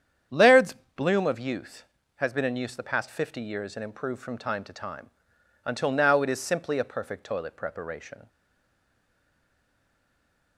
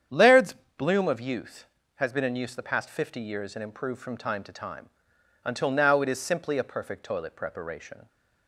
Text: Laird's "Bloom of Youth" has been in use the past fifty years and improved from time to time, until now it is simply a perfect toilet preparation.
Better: second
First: starts louder than the rest; strong; until 1.5 s; 8.5 dB // pauses between "Laird's" and "Bloom"; slight; at 0.7 s; 0.22 s long // stays silent after the last word; from 8.2 s on; 2.3 s long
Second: starts louder than the rest; strong; until 1.3 s; 8.5 dB // pauses between "Laird's" and "Bloom"; slight; at 0.5 s; 0.24 s long

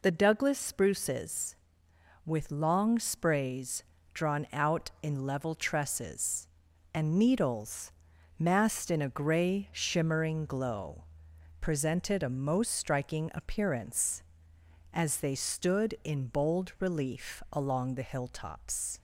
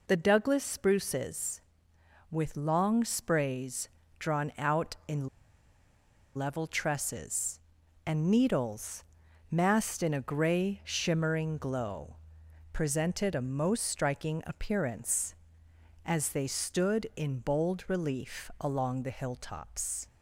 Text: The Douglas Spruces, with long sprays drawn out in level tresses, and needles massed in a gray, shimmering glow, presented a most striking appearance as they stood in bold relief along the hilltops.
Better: first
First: pauses between "sprays" and "drawn"; slight; at 3.8 s; 0.32 s long // pauses between "needles" and "massed"; noticeable; at 7.9 s; 0.48 s long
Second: pauses between "sprays" and "drawn"; slight; at 3.8 s; 0.32 s long // pauses between "in" and "level"; at 5.2 s; 1.0 s long // pauses between "needles" and "massed"; noticeable; at 9.0 s; 0.48 s long

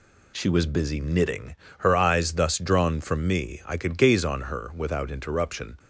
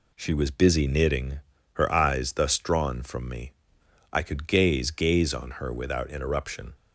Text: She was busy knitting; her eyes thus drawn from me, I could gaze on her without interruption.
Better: first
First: none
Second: says "gaze" twice; at 4.9 s

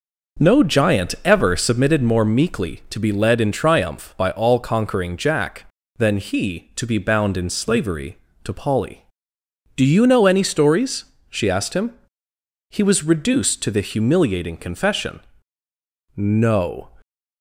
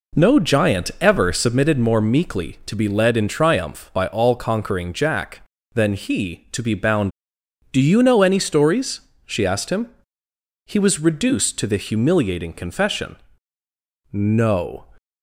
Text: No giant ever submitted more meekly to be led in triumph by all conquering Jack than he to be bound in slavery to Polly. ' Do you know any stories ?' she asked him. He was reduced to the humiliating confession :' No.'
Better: first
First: none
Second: skips "in slavery to Polly"; at 7.2 s

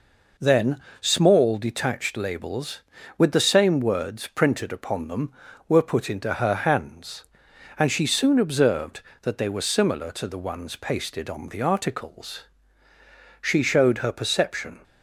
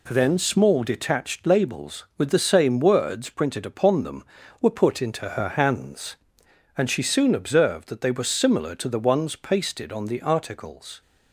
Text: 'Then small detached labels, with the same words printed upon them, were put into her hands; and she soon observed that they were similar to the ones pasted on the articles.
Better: second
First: pauses between "Then" and "small"; slight; at 0.8 s; 0.20 s long // goes on to say "She showed her perception"; from 13.4 s on; 1.4 s long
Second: none

